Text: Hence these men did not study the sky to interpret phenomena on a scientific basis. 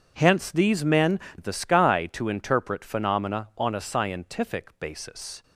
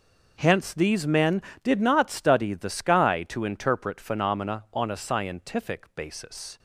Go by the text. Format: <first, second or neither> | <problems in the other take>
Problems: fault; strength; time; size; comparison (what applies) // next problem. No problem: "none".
second | skips "did not study"; at 1.2 s